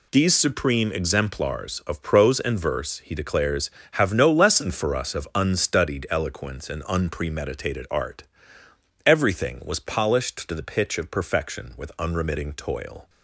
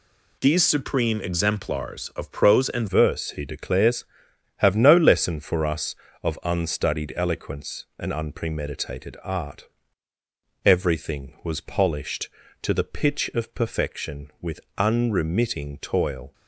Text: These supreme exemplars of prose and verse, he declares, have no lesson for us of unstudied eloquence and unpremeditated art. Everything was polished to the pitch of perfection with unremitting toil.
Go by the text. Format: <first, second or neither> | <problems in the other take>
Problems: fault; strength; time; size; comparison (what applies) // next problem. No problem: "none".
first | changes voice at "verse"; from 2.8 s on; 13.5 s long // pauses between "with" and "unremitting"; slight; at 14.6 s; 0.16 s long